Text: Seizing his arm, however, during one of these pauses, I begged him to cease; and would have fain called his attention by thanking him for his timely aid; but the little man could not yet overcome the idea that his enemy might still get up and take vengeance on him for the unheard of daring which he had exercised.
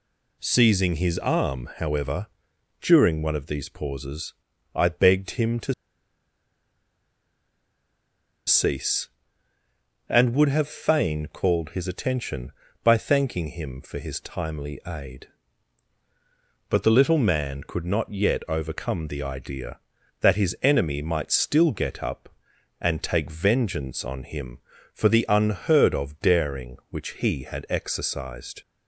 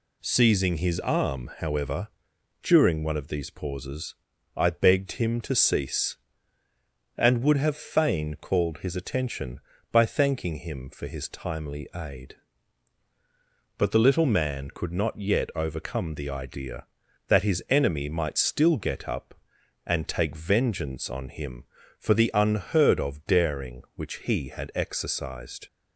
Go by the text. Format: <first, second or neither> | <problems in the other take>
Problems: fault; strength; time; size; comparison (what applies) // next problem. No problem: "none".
second | pauses between "to" and "cease"; strong; at 5.7 s; 2.7 s long